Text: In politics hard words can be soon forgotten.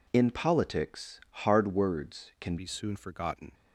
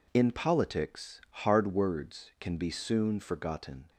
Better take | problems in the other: second | pauses between "politics" and "hard"; slight; at 1.2 s; 0.24 s long; slight in the second // changes voice at "be"; from 2.5 s on; 1.0 s long

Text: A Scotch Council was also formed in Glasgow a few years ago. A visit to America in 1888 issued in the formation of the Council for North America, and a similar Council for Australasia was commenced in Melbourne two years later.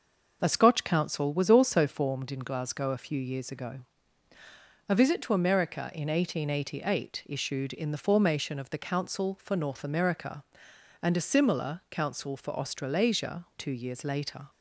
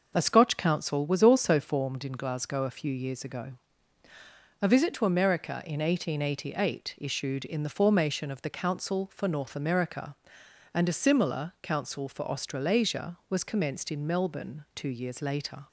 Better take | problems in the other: second | skips "was commenced in Melbourne"; at 13.5 s

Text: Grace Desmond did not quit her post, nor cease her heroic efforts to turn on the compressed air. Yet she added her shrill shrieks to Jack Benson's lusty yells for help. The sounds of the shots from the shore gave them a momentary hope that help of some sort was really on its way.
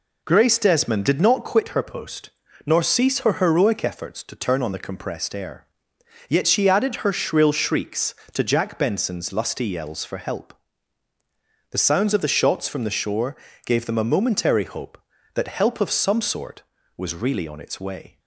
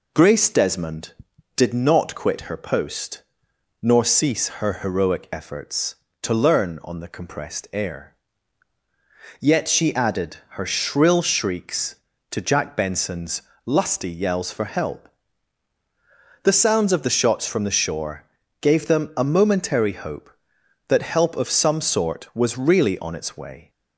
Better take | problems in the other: first | says "learn" for "turn"; at 6.3 s // pauses between "Benson's" and "lusty"; slight; at 13.4 s; 0.22 s long // pauses between "shore" and "gave"; at 18.2 s; 0.38 s long; slight in the first

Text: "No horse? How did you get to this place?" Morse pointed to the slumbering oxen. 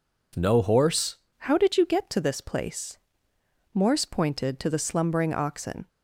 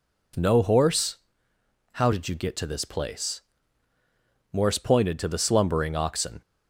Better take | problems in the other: second | changes voice at "How"; from 1.3 s on; 4.5 s long

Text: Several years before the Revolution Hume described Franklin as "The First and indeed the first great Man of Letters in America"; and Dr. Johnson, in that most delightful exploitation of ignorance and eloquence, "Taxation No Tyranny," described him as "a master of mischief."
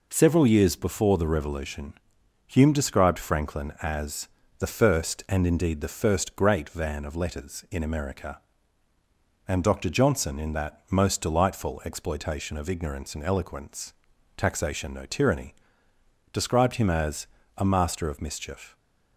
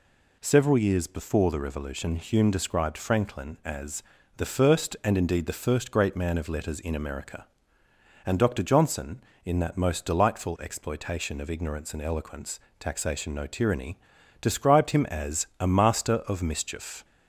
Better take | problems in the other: second | pauses between "Revolution" and "Hume"; noticeable; at 1.9 s; 0.54 s long // pauses between "as" and "The"; slight; at 4.2 s; 0.30 s long; slight in the second // says "Van" for "Man"; at 6.6 s // pauses between "as" and "a"; slight; at 17.2 s; 0.32 s long

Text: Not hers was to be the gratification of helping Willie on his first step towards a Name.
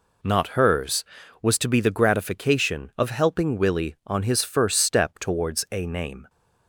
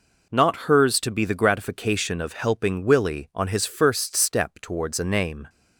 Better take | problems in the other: first | skips "was"; at 0.9 s

